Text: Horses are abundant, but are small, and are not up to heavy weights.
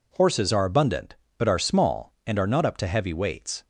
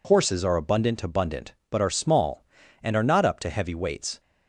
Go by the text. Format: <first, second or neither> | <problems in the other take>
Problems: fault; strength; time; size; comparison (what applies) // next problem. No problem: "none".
first | says "abundant" twice; at 1.0 s